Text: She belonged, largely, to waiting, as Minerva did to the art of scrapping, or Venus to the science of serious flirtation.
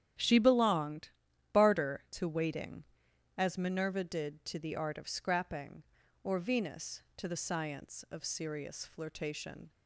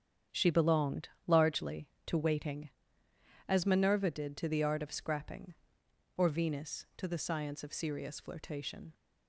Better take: second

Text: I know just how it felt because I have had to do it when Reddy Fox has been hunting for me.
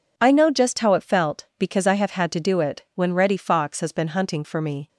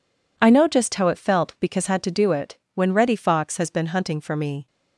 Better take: first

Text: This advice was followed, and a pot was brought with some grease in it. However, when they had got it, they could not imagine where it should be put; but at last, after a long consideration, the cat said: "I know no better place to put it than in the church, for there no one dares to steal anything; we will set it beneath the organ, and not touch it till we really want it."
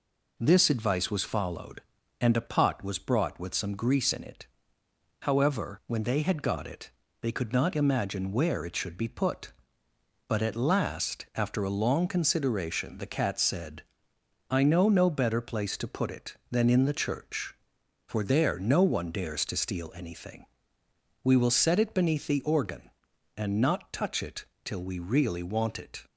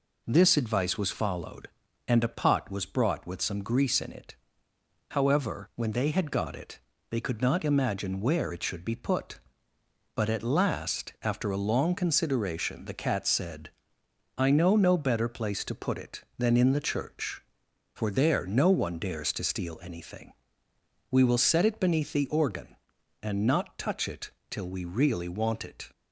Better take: neither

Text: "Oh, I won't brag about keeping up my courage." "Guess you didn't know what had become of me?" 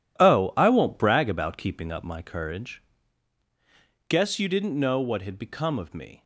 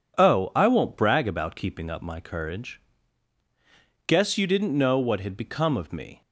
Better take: second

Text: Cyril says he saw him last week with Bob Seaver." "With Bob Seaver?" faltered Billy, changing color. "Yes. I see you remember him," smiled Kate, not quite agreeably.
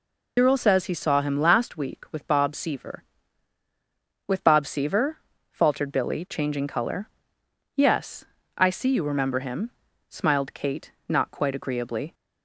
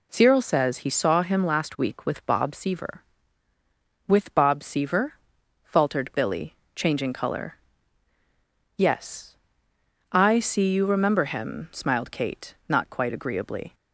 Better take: second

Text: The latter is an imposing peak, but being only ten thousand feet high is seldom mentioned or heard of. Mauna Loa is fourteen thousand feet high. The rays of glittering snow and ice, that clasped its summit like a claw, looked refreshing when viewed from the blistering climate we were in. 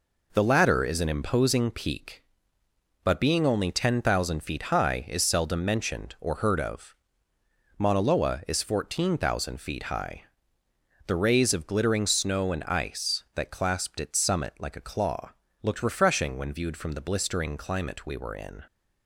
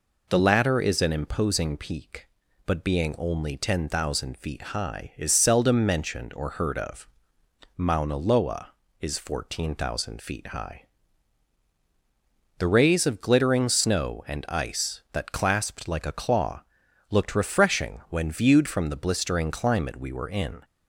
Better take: first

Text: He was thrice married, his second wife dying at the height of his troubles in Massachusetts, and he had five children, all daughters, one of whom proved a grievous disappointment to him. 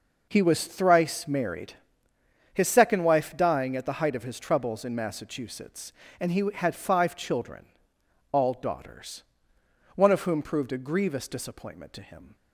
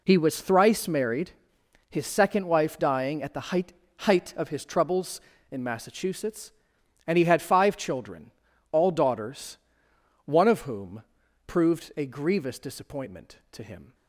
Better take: first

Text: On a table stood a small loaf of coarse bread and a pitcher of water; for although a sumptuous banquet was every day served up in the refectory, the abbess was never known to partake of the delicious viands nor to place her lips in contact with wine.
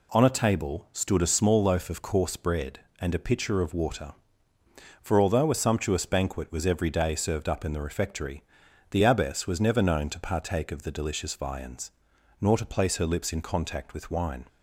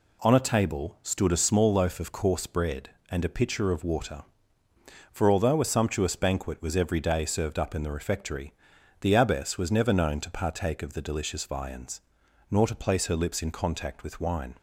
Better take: neither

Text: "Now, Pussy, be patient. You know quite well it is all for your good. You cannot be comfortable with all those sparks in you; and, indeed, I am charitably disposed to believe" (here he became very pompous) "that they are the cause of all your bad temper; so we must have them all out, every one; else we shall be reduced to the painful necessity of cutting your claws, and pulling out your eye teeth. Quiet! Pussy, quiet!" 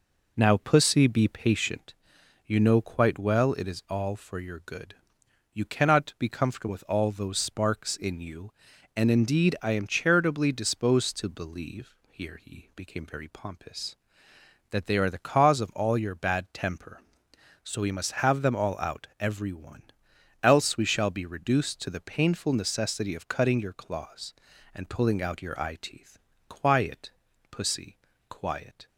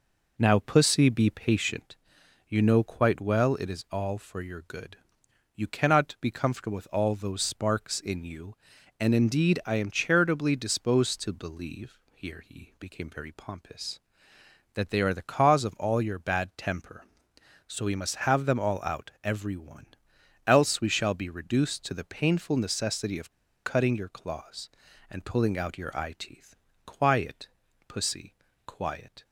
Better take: first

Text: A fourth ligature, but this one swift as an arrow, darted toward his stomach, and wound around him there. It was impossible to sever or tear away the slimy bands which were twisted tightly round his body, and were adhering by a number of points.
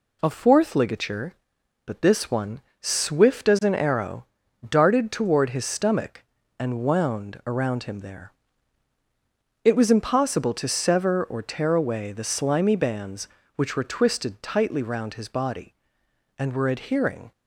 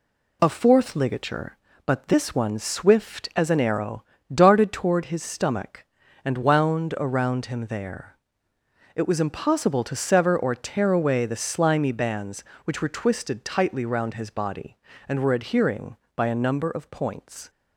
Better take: second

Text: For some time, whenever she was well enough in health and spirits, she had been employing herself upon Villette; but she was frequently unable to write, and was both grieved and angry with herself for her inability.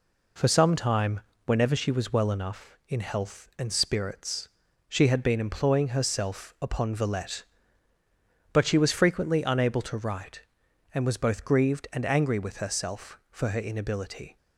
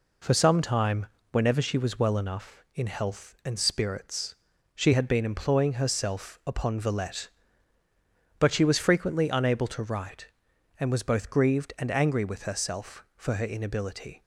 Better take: neither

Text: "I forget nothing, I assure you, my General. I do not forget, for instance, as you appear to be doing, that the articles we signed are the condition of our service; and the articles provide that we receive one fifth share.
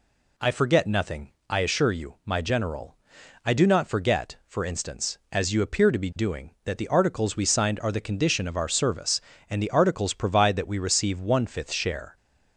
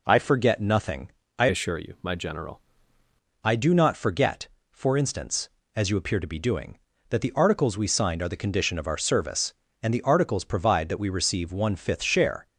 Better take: first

